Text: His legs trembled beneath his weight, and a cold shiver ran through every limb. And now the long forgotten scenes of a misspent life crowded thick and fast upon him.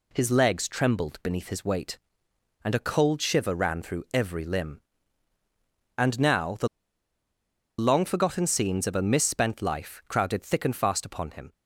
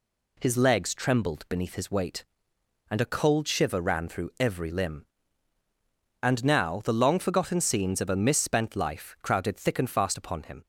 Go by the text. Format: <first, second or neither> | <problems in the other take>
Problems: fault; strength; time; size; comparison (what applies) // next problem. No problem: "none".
second | pauses between "the" and "long"; at 6.6 s; 1.1 s long